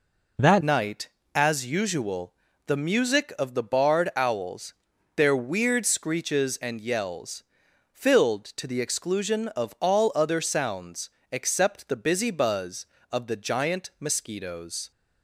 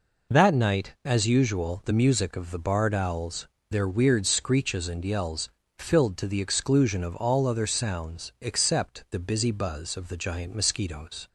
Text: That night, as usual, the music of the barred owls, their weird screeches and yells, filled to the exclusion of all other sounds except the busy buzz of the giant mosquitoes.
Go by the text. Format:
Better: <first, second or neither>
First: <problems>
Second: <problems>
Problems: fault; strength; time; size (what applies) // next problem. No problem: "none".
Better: second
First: changes voice at "night"; from 0.6 s on; 14.3 s long // pauses between "sounds" and "except"; slight; at 11.0 s; 0.24 s long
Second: none